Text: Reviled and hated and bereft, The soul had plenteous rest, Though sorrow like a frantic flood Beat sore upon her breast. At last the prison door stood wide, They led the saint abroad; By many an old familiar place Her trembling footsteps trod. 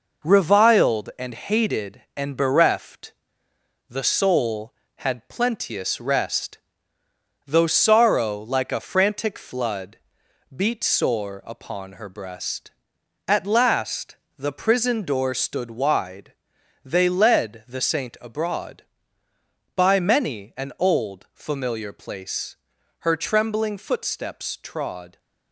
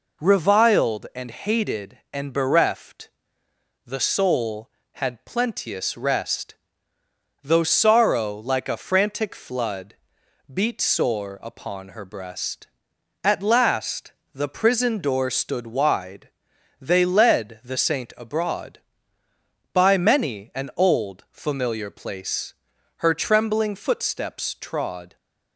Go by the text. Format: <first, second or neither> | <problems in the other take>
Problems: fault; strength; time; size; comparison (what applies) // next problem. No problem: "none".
second | gets quieter; noticeable; throughout; 5 dB // pauses between "flood" and "Beat"; noticeable; at 9.9 s; 0.56 s long; noticeable in the second // pauses between "last" and "the"; slight; at 14.1 s; 0.22 s long; slight in the second // pauses between "place" and "Her"; at 22.5 s; 0.44 s long; also in the second